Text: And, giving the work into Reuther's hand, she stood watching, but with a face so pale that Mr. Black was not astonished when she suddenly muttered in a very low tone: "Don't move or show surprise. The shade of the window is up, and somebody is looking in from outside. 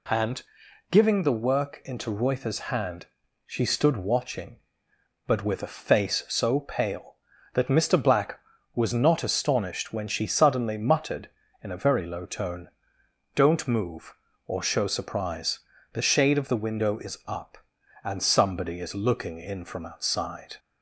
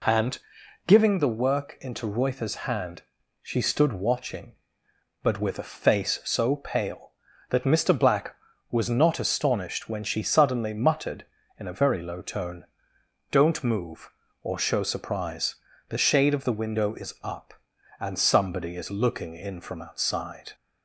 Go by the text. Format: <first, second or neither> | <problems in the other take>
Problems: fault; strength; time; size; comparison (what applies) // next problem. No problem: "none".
first | starts louder than the rest; slight; until 1.2 s; 2.5 dB